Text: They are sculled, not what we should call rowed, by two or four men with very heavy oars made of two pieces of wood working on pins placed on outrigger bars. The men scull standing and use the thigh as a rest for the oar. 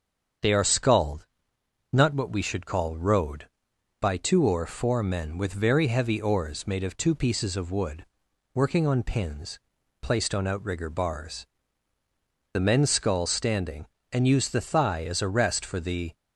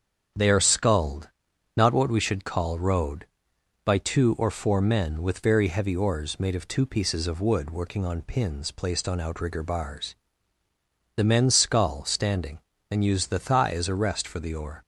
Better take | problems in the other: second | starts louder than the rest; strong; until 2.0 s; 7.5 dB; strong in the second // pauses between "wood" and "working"; noticeable; at 8.0 s; 0.48 s long // pauses between "pins" and "placed"; at 9.5 s; 0.42 s long // stops before "oar"; at 16.1 s

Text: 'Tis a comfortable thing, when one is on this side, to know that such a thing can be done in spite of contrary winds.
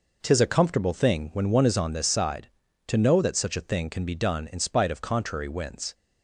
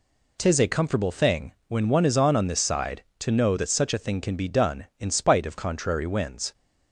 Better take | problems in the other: first | says "on" twice; at 2.3 s

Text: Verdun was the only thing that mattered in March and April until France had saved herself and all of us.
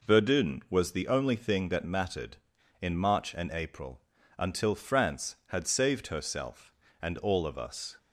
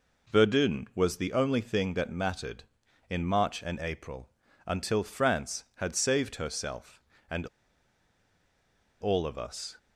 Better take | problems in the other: first | pauses between "April" and "until"; at 4.2 s; 0.38 s long; also in the first // pauses between "and" and "all"; strong; at 7.4 s; 1.5 s long

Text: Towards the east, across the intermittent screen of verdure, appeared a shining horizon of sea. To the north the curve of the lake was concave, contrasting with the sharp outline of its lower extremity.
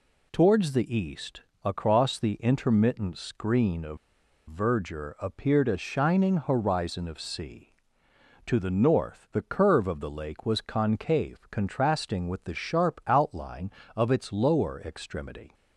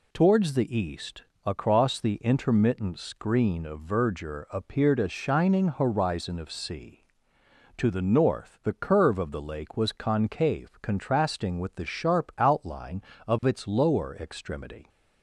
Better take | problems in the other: second | pauses between "of" and "verdure"; noticeable; at 3.9 s; 0.52 s long

